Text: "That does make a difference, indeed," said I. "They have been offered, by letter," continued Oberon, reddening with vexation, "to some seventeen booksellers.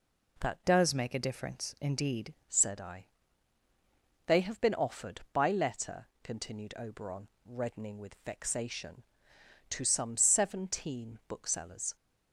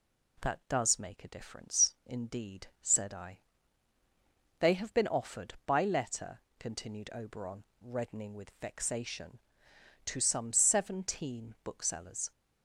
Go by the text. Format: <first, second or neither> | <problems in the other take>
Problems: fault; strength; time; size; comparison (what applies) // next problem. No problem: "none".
second | changes voice from "does" to "indeed"; from 0.6 to 2.3 s; 1.7 s long